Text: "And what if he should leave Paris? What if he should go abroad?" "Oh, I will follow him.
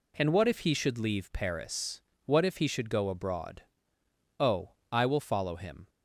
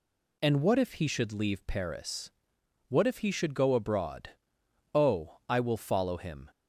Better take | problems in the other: neither | none

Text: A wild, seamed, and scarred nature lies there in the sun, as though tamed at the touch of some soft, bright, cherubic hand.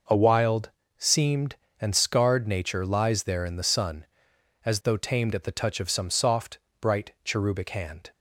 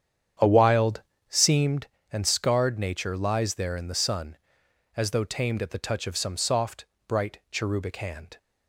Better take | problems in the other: first | starts louder than the rest; strong; until 1.9 s; 8.5 dB

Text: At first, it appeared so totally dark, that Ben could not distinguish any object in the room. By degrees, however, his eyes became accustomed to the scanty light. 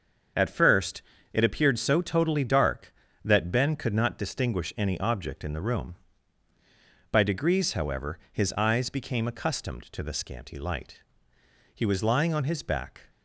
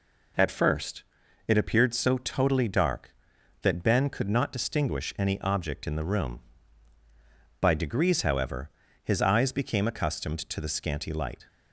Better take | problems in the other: second | starts louder than the rest; until 1.6 s; 6.5 dB // goes on to say "He was lying on his back"; from 11.7 s on; 1.3 s long

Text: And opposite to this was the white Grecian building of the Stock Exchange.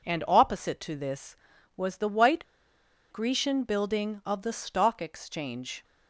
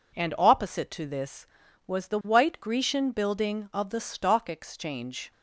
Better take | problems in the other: second | pauses between "white" and "Grecian"; noticeable; at 2.4 s; 0.66 s long

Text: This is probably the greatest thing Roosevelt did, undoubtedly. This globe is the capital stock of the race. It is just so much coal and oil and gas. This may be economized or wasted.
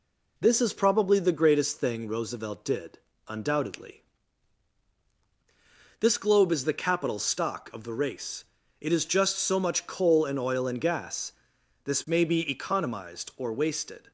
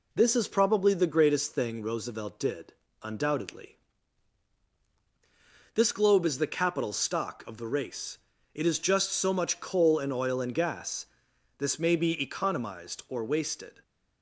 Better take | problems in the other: neither | none

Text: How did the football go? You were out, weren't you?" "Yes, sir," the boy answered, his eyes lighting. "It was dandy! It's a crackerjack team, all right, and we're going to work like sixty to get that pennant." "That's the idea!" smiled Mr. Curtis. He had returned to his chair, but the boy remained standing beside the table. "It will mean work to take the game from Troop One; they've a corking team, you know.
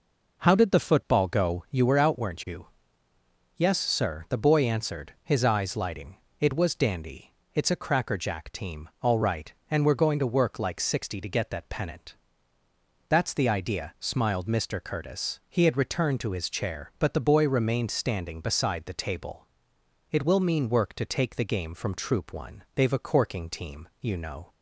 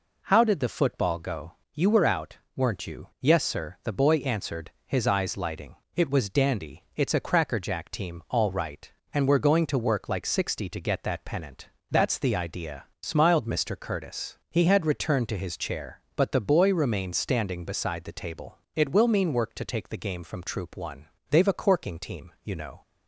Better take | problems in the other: neither | none

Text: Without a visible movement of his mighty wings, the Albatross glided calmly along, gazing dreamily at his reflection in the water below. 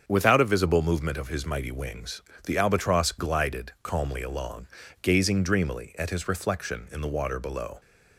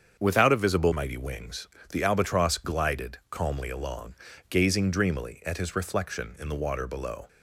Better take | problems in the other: first | starts louder than the rest; strong; until 1.2 s; 7.5 dB; also in the first // skips "movement of his"; at 0.9 s

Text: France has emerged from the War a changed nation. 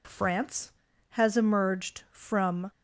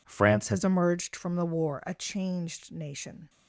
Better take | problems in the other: second | stops before "the War a changed nation"; at 2.7 s

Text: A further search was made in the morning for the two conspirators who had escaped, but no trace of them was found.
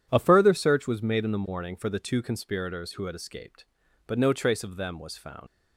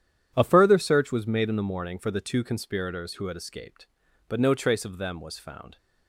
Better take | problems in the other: second | leaves "found" unfinished; at 5.4 s; 85 ms

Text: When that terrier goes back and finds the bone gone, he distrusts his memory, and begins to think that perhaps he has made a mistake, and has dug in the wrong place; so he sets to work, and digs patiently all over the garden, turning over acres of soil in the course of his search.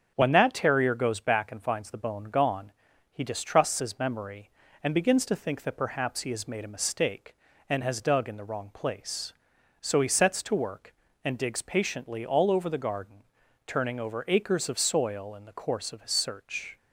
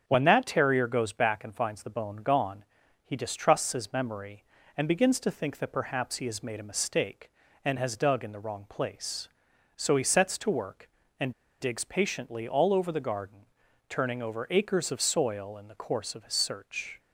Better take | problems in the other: first | starts louder than the rest; strong; until 1.1 s; 7 dB; strong in the first // pauses between "and" and "digs"; slight; at 11.3 s; 0.27 s long

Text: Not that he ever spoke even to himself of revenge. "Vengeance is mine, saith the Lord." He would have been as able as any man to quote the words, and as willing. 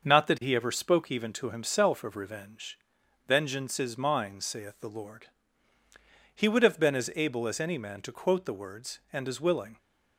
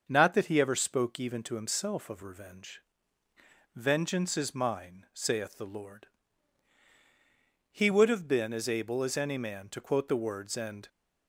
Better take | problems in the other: first | starts louder than the rest; until 1.0 s; 6.5 dB; also in the first // stops before "as willing"; at 10.8 s

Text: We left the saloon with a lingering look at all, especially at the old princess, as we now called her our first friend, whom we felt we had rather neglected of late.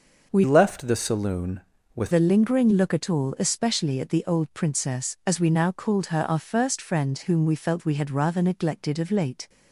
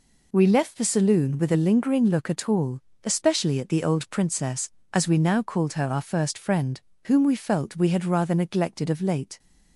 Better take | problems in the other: second | changes voice from "left" to "with"; from 0.4 to 2.1 s; 1.7 s long

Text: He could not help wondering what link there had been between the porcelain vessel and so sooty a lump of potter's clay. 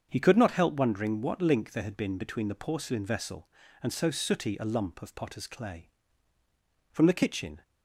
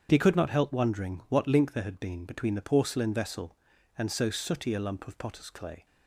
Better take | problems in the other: second | starts louder than the rest; until 1.1 s; 7 dB; strong in the second // goes on to say "From the kitchen"; noticeable; from 6.9 s on; 0.72 s long

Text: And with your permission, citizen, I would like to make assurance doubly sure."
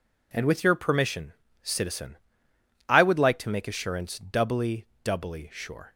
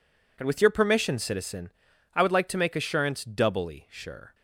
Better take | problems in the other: second | says "doubly" twice; at 5.0 s

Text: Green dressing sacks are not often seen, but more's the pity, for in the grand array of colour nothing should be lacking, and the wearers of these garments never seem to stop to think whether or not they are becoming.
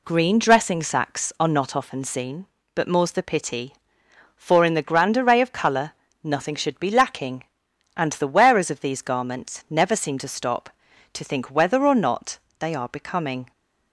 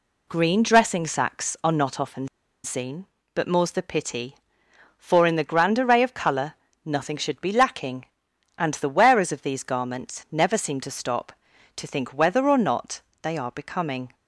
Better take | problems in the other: first | pauses between "often" and "seen"; slight; at 2.2 s; 0.36 s long // pauses between "colour" and "nothing"; slight; at 6.5 s; 0.32 s long; slight in the first // pauses between "not" and "they"; slight; at 13.0 s; 0.18 s long; slight in the first

